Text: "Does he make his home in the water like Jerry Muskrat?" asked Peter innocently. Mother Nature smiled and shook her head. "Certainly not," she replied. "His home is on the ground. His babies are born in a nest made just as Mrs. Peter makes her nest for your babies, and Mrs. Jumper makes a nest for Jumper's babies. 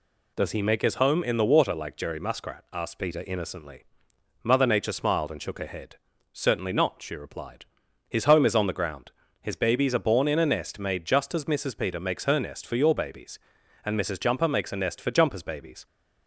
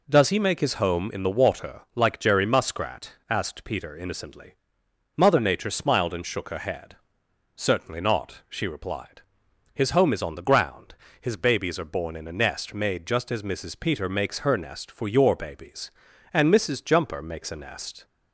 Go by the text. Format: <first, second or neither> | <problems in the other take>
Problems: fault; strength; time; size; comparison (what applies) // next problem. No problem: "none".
first | stops before "for Jumper's babies"; at 18.0 s